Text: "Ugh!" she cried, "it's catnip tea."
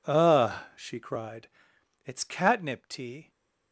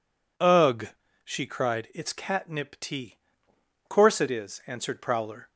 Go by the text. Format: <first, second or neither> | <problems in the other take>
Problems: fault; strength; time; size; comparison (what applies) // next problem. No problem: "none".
first | goes on to say "Course it is answered Prowler"; from 3.8 s on; 1.6 s long